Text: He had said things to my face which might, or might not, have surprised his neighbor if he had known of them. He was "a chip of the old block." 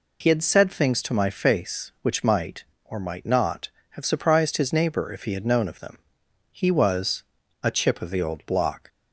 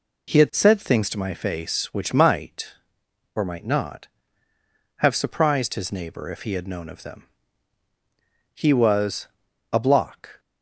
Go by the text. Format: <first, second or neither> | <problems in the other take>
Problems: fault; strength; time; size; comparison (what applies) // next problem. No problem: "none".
first | pauses between "was" and "a"; noticeable; at 9.2 s; 0.46 s long; also in the first // skips "chip of the old"; at 9.7 s